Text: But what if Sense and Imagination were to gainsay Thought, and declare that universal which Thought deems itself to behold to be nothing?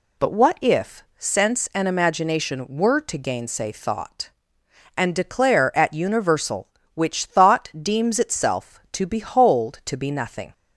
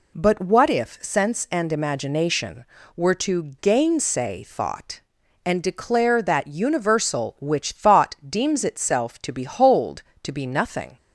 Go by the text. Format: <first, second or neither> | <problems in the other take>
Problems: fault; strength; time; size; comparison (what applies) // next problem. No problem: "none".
second | says "at" for "that"; at 5.7 s